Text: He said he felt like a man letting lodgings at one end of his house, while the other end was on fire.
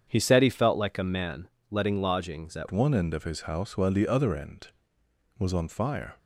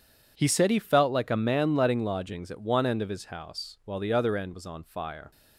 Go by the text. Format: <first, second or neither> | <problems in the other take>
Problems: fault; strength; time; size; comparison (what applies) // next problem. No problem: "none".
second | starts louder than the rest; strong; until 1.0 s; 7.5 dB // pauses between "man" and "letting"; slight; at 1.4 s; 0.20 s long // changes voice at "one"; from 2.7 s on; 3.4 s long